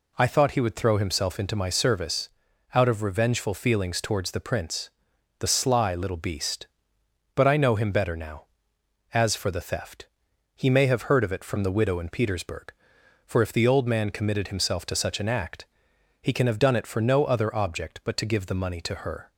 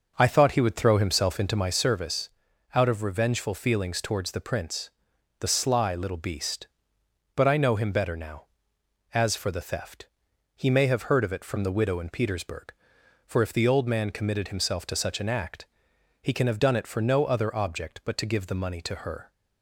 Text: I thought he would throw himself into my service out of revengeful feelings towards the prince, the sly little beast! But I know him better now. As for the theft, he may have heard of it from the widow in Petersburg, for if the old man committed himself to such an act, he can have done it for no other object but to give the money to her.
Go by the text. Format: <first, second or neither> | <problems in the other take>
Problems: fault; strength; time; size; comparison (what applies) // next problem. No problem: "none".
first | starts louder than the rest; noticeable; until 1.8 s; 6 dB // pauses between "service" and "out"; noticeable; at 2.2 s; 0.46 s long; noticeable in the first